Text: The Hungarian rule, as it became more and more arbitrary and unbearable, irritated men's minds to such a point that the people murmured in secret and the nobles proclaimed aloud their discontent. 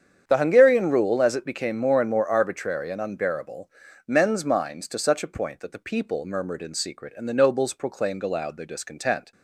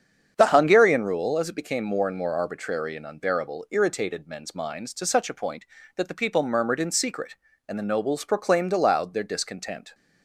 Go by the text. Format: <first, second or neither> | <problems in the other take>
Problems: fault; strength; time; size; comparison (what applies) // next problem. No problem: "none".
second | starts louder than the rest; strong; until 1.2 s; 8 dB; strong in the second // skips "irritated"; at 3.8 s